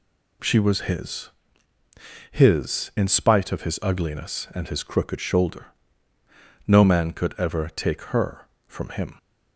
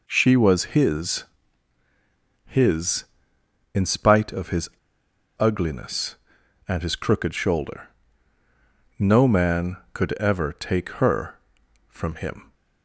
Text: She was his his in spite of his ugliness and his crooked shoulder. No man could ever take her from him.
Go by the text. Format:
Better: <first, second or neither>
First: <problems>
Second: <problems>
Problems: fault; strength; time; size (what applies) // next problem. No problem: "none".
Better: first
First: pauses between "his" and "his"; at 1.2 s; 1.0 s long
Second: pauses between "his" and "his"; at 1.2 s; 1.2 s long // pauses between "his" and "ugliness"; noticeable; at 4.6 s; 0.69 s long